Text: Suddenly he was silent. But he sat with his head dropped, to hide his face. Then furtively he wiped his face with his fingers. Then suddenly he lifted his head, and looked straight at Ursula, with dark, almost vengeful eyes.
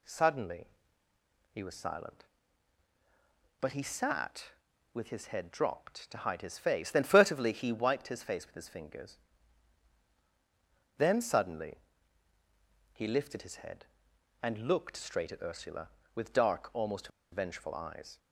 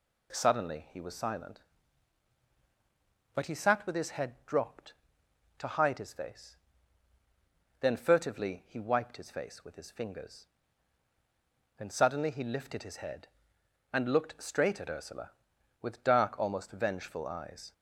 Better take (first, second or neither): second